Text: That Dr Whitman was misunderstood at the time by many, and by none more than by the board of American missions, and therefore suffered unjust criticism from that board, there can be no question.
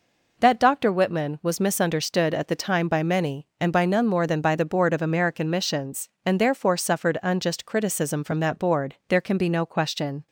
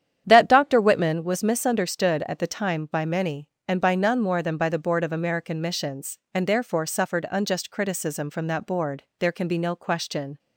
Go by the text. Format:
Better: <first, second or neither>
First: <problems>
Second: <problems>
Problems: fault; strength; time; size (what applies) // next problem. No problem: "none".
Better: first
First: none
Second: starts louder than the rest; strong; until 1.3 s; 9.5 dB